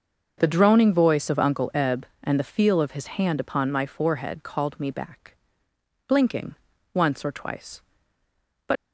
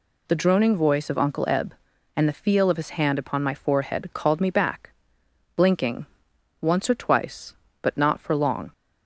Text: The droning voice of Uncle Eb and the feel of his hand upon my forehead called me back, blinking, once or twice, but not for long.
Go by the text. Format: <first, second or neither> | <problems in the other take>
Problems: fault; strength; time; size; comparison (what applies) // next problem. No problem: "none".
second | starts louder than the rest; until 1.4 s; 6.5 dB // stops before "not for long"; at 8.7 s